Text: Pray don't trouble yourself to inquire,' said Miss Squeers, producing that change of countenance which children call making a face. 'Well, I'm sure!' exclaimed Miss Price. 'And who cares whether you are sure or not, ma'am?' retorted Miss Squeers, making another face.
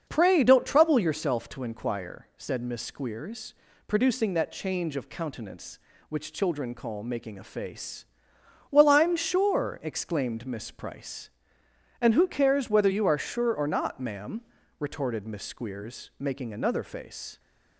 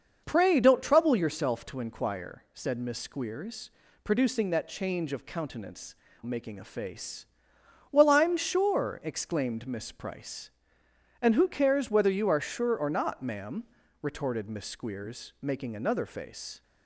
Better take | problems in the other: first | starts louder than the rest; until 1.2 s; 6 dB; also in the first // skips "which children call"; at 6.0 s

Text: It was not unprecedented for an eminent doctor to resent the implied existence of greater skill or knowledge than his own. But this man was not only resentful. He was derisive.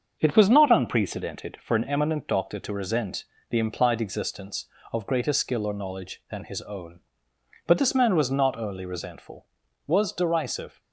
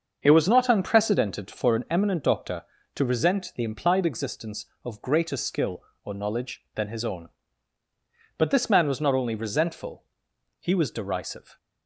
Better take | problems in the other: second | starts louder than the rest; until 1.2 s; 7 dB; also in the second // pauses between "resent" and "the"; slight; at 3.2 s; 0.26 s long // skips "He"; at 9.6 s

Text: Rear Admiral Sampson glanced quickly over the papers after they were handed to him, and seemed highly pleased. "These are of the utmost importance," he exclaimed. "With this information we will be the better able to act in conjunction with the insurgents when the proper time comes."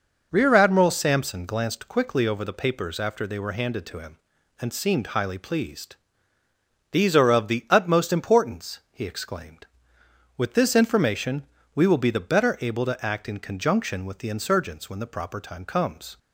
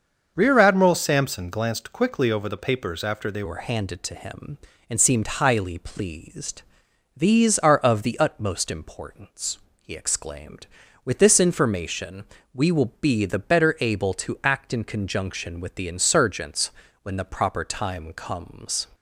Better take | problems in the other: first | starts louder than the rest; until 1.3 s; 6.5 dB // changes voice at "were"; from 3.4 s on; 15.4 s long // pauses between "information" and "we"; slight; at 12.2 s; 0.30 s long; slight in the first // pauses between "insurgents" and "when"; slight; at 16.7 s; 0.32 s long

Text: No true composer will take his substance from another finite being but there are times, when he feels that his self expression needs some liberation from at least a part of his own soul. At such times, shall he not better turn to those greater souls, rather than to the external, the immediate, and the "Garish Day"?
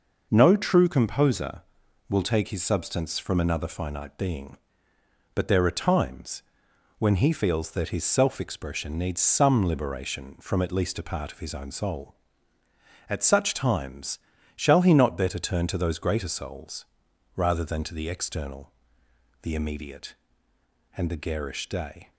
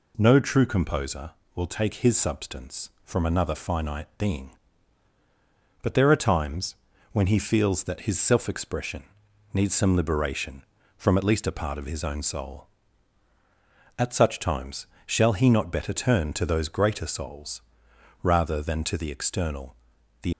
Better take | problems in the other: first | pauses between "expression" and "needs"; noticeable; at 9.0 s; 0.50 s long // stops before "immediate and the Garish Day"; at 20.3 s

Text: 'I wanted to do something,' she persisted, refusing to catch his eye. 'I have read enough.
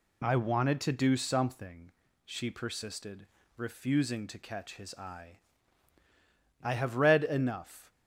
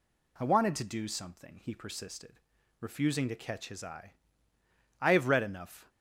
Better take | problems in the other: first | says "he" for "she"; at 1.6 s

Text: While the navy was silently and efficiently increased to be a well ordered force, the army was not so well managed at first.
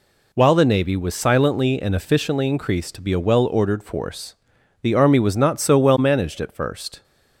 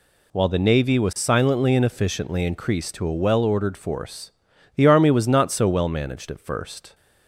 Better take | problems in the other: first | skips "be"; at 3.0 s

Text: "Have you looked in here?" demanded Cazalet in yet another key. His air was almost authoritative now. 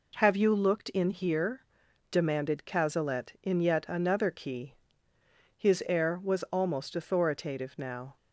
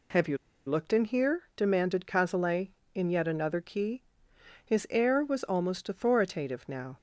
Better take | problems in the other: first | pauses between "you" and "looked"; slight; at 0.3 s; 0.31 s long

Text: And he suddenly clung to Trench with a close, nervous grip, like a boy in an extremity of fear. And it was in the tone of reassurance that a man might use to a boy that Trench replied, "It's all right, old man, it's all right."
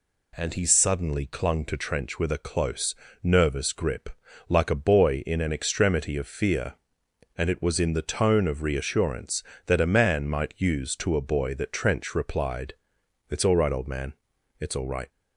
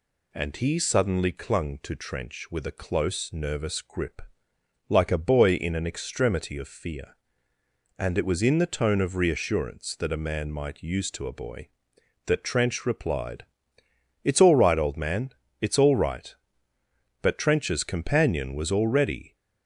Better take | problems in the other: first | goes on to say "But Trench's companion was already"; strong; from 17.2 s on; 2.1 s long

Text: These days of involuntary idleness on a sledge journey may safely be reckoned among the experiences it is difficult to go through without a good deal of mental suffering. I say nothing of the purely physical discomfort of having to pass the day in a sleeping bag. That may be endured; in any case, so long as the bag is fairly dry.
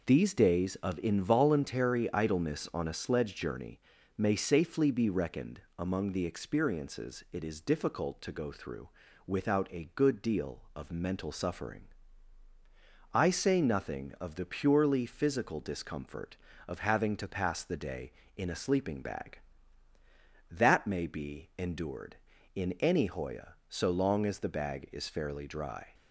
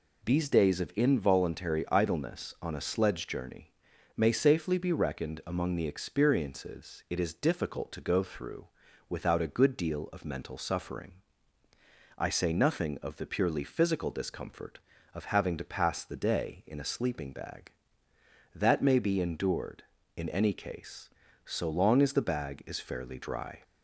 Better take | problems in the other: second | pauses between "journey" and "may"; at 3.7 s; 0.38 s long; noticeable in the second // pauses between "reckoned" and "among"; slight; at 5.6 s; 0.16 s long // pauses between "through" and "without"; slight; at 8.8 s; 0.36 s long; also in the second // says "hoya" for "case"; at 23.0 s

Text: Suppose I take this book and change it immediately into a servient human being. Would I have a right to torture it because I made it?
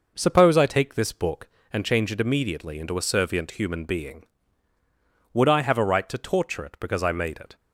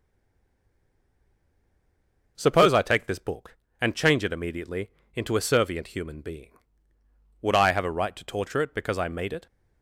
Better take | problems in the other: first | stays silent before the first word; until 2.3 s; 2.3 s long // pauses between "immediately" and "into"; slight; at 4.8 s; 0.24 s long

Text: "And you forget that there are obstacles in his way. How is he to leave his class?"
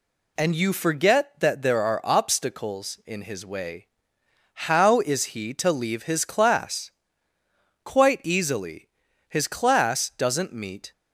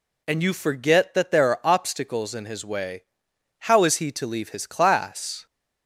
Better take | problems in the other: second | goes on to say "Quite easily His class doesn't meet"; strong; from 7.8 s on; 3.0 s long

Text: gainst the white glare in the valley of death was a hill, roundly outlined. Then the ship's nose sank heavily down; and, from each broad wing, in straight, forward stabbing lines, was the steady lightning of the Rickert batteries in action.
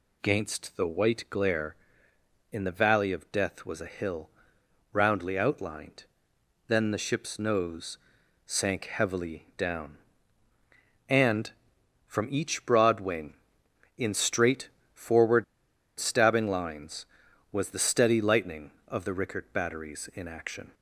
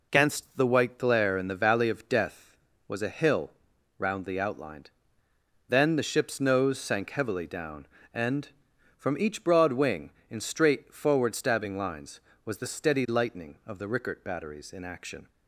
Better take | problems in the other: second | pauses between "nose" and "sank"; noticeable; at 7.9 s; 0.48 s long // pauses between "forward" and "stabbing"; noticeable; at 15.4 s; 0.55 s long

